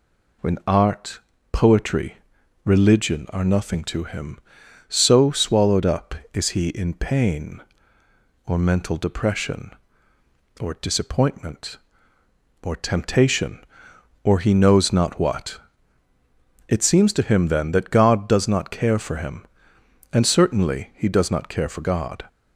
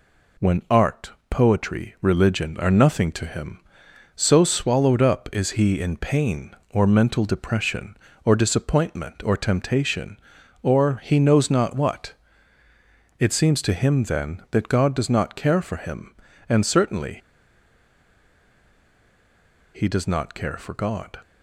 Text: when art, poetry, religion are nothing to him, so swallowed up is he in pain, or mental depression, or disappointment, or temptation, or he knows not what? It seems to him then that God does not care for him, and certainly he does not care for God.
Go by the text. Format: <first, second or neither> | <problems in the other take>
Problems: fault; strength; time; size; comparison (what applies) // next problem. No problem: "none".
first | pauses between "certainly" and "he"; strong; at 17.1 s; 2.5 s long